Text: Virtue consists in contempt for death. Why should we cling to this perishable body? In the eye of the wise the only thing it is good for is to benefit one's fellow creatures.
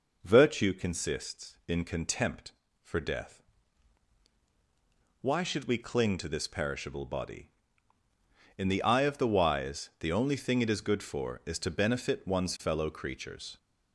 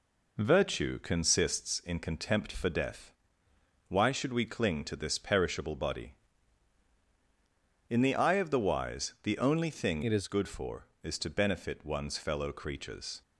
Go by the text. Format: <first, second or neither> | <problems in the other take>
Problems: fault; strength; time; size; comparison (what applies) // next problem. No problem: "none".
first | changes voice from "it" to "is"; from 10.0 to 10.2 s; 0.2 s long